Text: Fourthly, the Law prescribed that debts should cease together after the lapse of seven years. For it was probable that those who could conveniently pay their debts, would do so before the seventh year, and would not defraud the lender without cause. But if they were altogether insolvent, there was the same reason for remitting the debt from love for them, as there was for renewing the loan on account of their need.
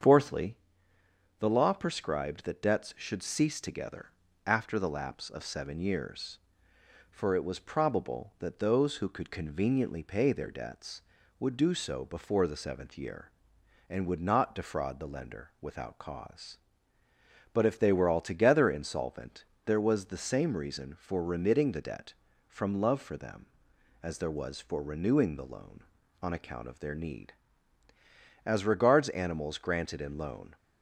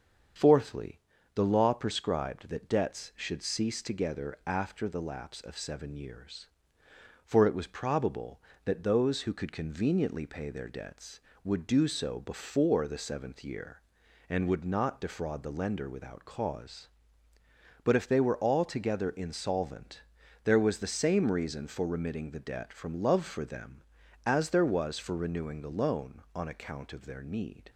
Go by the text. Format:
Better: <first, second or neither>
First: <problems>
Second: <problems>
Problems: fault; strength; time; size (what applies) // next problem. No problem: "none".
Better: second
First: starts louder than the rest; strong; until 1.8 s; 7.5 dB // pauses between "together" and "after"; at 4.0 s; 0.38 s long // goes on to say "As regards animals granted in loan"; strong; from 28.4 s on; 2.1 s long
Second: starts louder than the rest; strong; until 1.7 s; 7 dB